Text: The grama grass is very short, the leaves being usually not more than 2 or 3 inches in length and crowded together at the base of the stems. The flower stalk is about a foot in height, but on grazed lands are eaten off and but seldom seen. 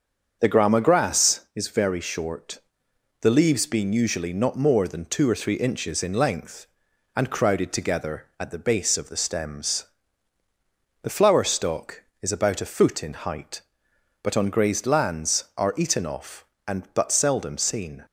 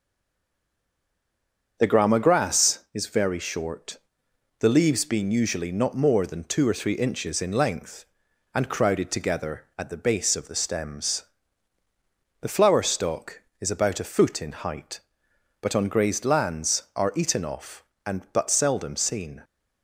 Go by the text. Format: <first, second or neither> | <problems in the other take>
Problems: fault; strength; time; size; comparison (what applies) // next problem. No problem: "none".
first | stays silent before the first word; noticeable; until 1.7 s; 1.7 s long // starts louder than the rest; until 2.8 s; 7 dB; also in the first